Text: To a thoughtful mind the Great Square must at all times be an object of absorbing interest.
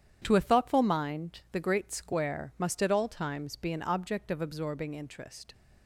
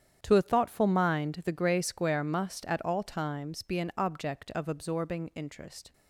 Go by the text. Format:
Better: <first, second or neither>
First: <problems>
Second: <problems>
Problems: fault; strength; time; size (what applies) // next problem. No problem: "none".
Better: first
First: starts louder than the rest; strong; until 1.2 s; 9.5 dB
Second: starts louder than the rest; strong; until 1.2 s; 9.5 dB // says "Grey" for "Great"; at 1.5 s